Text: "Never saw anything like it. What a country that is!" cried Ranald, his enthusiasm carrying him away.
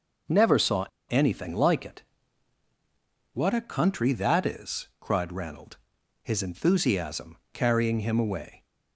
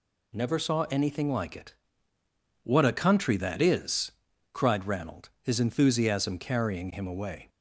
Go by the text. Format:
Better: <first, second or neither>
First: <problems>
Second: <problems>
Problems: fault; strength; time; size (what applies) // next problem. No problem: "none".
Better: second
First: pauses between "saw" and "anything"; slight; at 0.8 s; 0.22 s long // pauses between "enthusiasm" and "carrying"; slight; at 7.3 s; 0.18 s long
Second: none